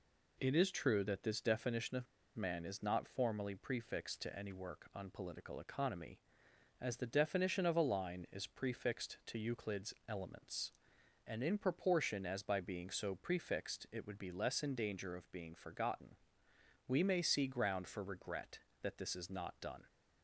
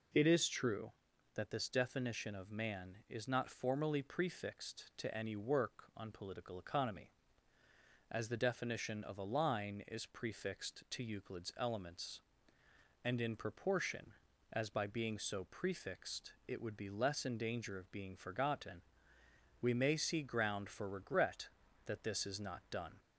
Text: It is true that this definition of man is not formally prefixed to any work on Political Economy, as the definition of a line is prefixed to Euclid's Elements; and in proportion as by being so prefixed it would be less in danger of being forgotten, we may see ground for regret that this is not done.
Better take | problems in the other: second | pauses between "of" and "man"; slight; at 2.0 s; 0.30 s long

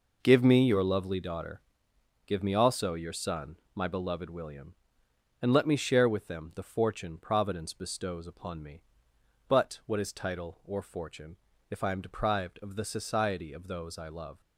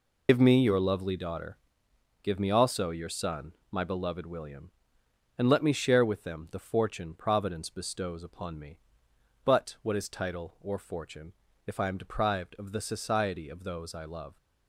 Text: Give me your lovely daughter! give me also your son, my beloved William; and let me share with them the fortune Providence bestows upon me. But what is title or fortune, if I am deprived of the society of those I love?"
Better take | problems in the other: first | loses the start of "Give"; at 0.2 s; 105 ms

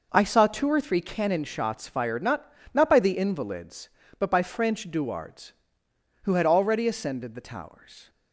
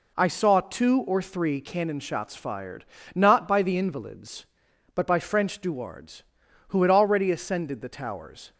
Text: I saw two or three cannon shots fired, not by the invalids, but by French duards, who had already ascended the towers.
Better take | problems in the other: second | says "not" twice; at 2.7 s

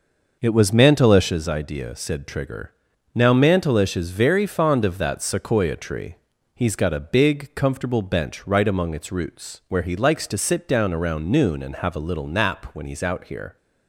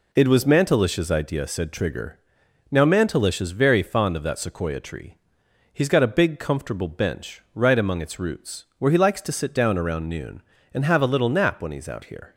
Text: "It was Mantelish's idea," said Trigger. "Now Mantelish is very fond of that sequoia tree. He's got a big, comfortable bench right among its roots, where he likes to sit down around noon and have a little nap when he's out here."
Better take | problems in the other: second | starts louder than the rest; noticeable; until 1.5 s; 6 dB

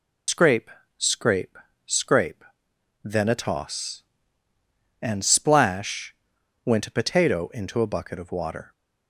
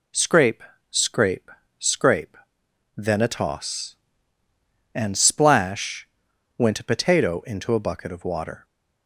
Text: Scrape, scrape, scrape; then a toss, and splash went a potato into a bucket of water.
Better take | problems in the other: second | loses the start of "Scrape"; at 0.2 s; 85 ms // pauses between "splash" and "went"; noticeable; at 6.1 s; 0.48 s long; noticeable in the second

